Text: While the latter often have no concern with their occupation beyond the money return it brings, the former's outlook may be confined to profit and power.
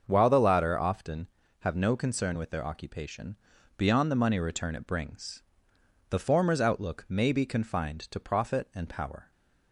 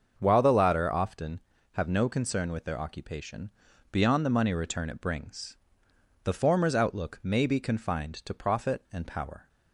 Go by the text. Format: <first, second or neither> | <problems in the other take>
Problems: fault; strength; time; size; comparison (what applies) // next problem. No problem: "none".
neither | starts louder than the rest; the same in both // pauses between "occupation" and "beyond"; the same in both